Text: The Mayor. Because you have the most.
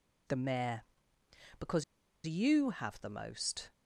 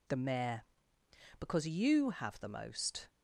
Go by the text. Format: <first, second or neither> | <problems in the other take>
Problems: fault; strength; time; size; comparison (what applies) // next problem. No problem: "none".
second | pauses between "Because" and "you"; at 1.8 s; 0.42 s long